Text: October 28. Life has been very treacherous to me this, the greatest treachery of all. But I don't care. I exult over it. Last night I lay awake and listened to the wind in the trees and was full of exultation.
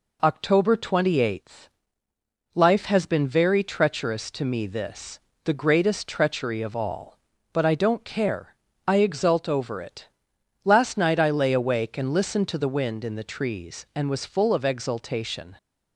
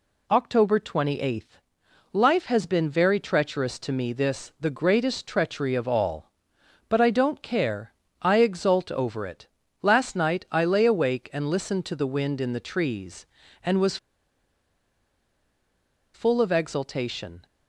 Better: first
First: none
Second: pauses between "was" and "full"; strong; at 13.9 s; 2.1 s long

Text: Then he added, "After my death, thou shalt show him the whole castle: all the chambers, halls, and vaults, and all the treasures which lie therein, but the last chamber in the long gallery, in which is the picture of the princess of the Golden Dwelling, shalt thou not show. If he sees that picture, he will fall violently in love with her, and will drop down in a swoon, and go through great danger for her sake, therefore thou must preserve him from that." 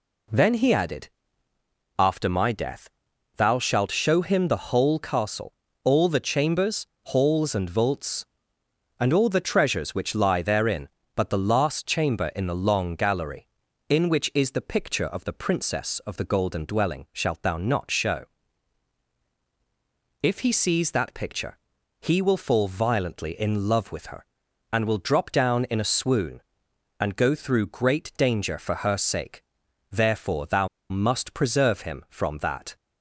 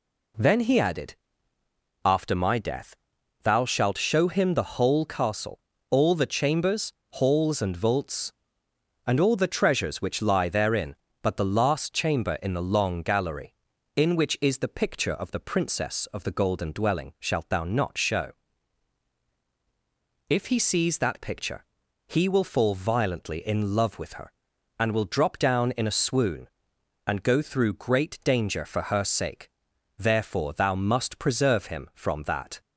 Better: second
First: pauses between "thou" and "must"; slight; at 30.6 s; 0.22 s long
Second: none

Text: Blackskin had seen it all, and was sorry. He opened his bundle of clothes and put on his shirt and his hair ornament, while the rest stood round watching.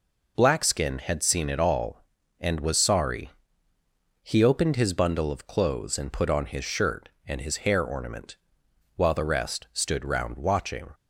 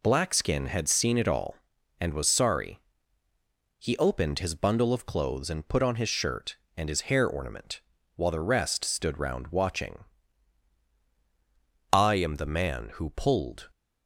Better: first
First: none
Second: goes on to say "I am the man who pulled"; strong; from 11.9 s on; 1.7 s long

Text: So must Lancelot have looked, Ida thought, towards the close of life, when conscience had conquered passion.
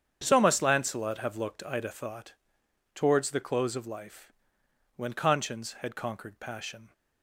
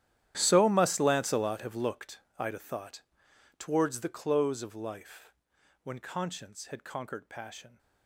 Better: first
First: starts louder than the rest; strong; until 1.2 s; 8 dB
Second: gets quieter; strong; throughout; 19 dB // starts louder than the rest; strong; until 1.3 s; 11.5 dB

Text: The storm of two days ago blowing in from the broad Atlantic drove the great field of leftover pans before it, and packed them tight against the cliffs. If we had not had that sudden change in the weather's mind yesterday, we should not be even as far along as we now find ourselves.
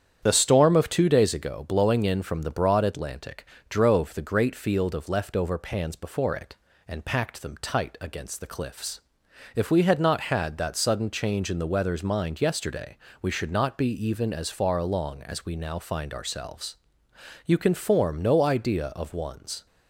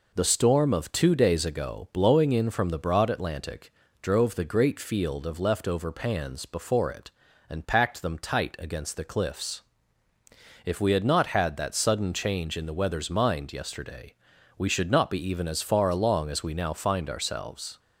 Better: second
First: starts louder than the rest; strong; until 1.2 s; 9 dB // pauses between "Atlantic" and "drove"; slight; at 3.4 s; 0.24 s long // goes on to say "You can form no idea of one's"; strong; from 17.4 s on; 2.2 s long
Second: pauses between "Atlantic" and "drove"; slight; at 3.7 s; 0.30 s long

